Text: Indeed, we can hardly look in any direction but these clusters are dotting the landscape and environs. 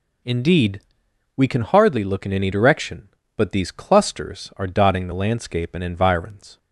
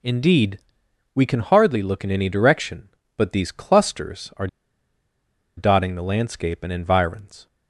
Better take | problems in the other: first | pauses between "are" and "dotting"; at 4.4 s; 1.1 s long

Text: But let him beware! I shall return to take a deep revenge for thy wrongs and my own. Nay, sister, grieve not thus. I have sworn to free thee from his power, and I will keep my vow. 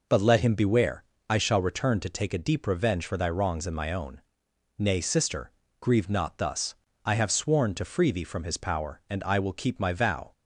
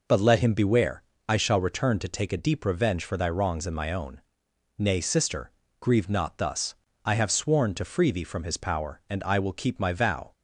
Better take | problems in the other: neither | none

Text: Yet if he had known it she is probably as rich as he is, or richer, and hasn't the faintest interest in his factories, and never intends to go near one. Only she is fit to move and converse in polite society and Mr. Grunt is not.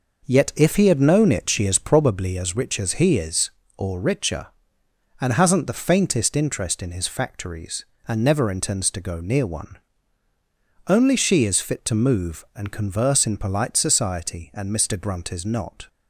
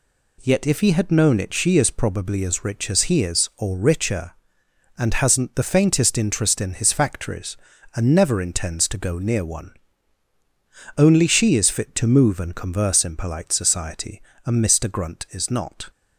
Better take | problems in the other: second | starts louder than the rest; noticeable; until 2.1 s; 5.5 dB

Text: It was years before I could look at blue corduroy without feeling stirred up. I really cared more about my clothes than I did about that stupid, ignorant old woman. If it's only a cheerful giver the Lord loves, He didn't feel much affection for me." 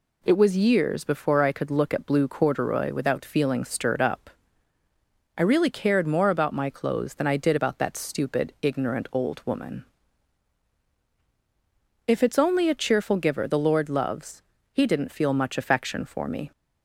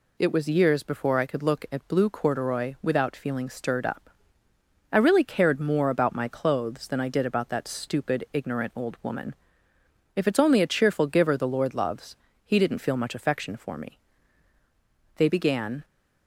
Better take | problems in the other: first | goes on to say "They began"; noticeable; from 15.1 s on; 0.66 s long

